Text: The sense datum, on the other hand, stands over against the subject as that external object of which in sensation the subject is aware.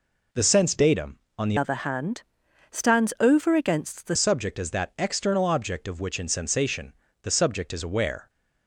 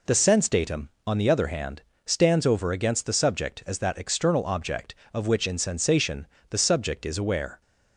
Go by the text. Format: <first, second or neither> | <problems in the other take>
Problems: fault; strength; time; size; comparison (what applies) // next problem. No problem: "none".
second | changes voice from "other" to "the"; from 1.5 to 4.1 s; 2.6 s long // pauses between "sensation" and "the"; slight; at 6.9 s; 0.30 s long; slight in the second